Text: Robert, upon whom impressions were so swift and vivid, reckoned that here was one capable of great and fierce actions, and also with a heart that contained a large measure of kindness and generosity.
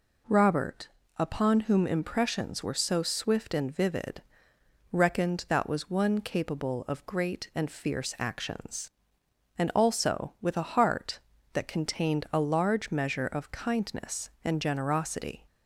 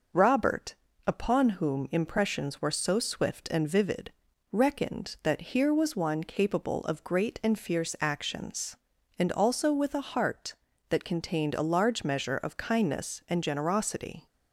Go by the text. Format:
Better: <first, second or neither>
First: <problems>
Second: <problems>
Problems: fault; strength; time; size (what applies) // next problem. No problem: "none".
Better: second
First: skips "here"; at 5.6 s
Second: none